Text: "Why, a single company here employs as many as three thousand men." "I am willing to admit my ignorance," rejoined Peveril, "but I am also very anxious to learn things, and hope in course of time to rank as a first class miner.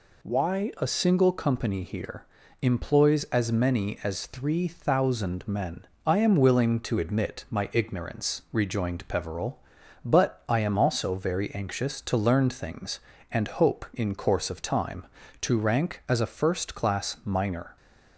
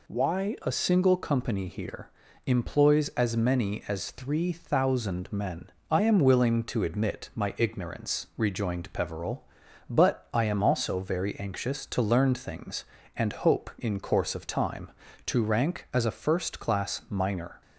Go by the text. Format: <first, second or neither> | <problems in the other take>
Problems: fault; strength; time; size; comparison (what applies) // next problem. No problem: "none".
neither | pauses between "here" and "employs"; slight; the same in both